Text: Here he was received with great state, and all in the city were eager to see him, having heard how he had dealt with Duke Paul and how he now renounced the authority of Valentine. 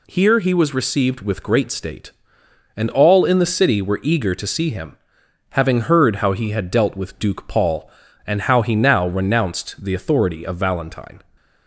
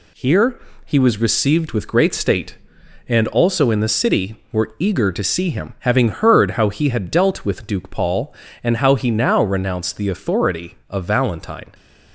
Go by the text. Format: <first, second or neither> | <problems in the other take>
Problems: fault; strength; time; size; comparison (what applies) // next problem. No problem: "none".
first | pauses between "Here" and "he"; slight; at 0.6 s; 0.26 s long // says "also" for "all"; at 3.2 s